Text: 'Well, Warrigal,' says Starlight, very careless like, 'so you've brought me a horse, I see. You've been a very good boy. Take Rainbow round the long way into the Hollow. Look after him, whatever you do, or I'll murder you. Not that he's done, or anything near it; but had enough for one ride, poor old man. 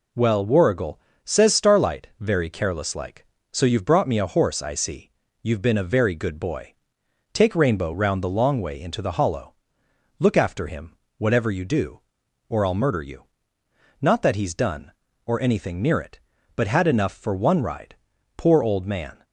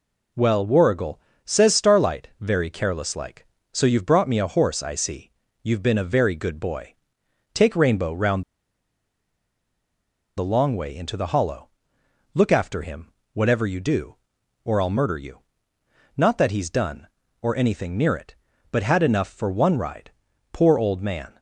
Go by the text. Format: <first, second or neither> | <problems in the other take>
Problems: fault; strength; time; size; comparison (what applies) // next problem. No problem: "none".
first | pauses between "round" and "the"; strong; at 8.4 s; 1.9 s long